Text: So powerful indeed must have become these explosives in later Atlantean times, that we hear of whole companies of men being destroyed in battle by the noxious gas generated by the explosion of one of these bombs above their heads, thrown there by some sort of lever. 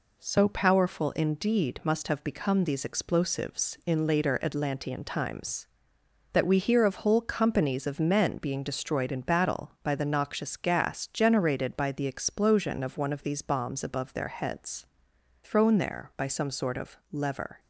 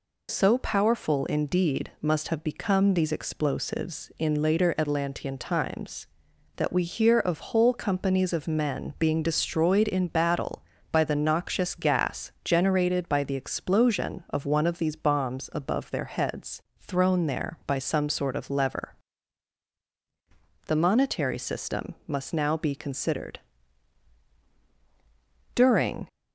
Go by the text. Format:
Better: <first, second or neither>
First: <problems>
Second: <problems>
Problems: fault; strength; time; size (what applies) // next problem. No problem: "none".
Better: first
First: none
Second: goes on to say "The monetary system must now be considered During"; strong; from 20.6 s on; 5.4 s long